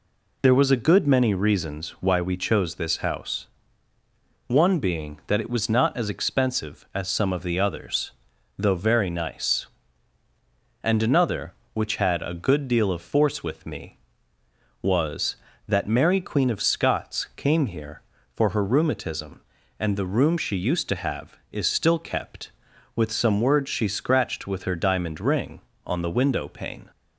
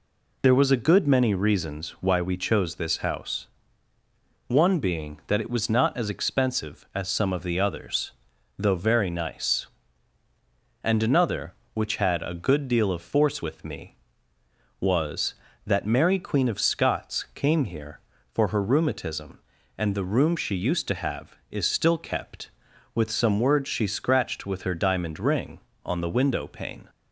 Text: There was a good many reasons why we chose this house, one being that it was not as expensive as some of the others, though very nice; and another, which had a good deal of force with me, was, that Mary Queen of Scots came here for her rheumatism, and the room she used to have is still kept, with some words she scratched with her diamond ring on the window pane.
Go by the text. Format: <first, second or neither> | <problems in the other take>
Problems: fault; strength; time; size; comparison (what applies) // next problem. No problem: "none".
neither | none